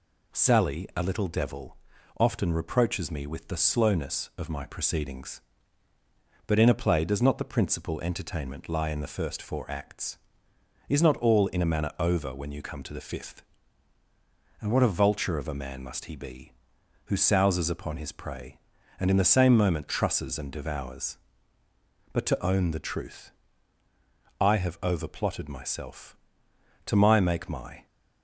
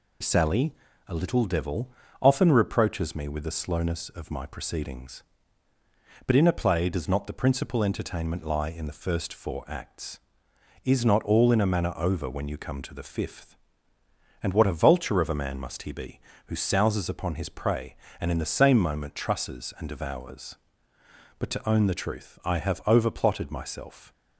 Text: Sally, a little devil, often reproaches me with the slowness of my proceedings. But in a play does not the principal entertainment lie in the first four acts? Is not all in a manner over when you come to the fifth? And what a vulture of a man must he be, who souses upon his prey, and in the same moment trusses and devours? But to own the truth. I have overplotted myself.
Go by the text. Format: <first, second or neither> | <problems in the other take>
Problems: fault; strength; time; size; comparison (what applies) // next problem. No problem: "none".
second | goes on to say "To my make my"; noticeable; from 26.8 s on; 1.0 s long